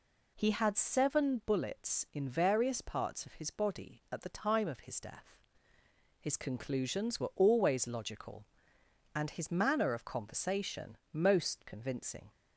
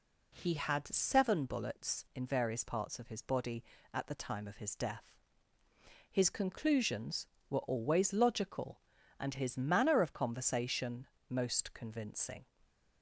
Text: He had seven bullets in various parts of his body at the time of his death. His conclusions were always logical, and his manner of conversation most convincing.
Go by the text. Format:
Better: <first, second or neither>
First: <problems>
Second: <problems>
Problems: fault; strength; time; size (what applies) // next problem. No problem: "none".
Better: neither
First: pauses between "conversation" and "most"; slight; at 10.9 s; 0.16 s long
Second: pauses between "conversation" and "most"; slight; at 11.0 s; 0.24 s long